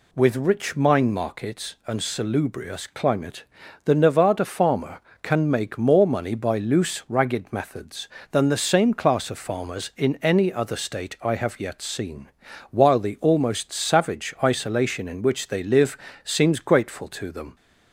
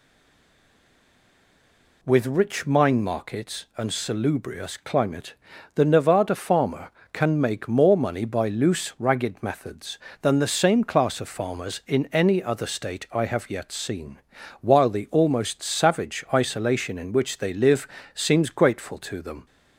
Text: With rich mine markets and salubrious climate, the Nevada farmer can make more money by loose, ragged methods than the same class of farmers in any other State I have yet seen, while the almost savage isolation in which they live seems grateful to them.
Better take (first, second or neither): first